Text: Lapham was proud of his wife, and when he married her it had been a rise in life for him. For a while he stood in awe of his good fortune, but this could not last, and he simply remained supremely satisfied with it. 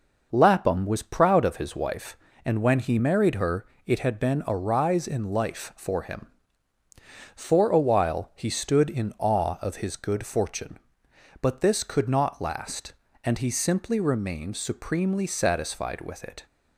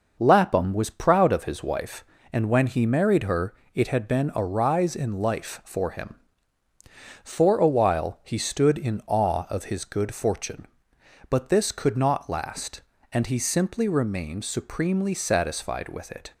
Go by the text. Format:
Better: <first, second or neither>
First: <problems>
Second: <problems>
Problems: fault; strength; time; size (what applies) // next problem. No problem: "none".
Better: neither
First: pauses between "her" and "it"; slight; at 3.6 s; 0.20 s long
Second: pauses between "her" and "it"; slight; at 3.5 s; 0.20 s long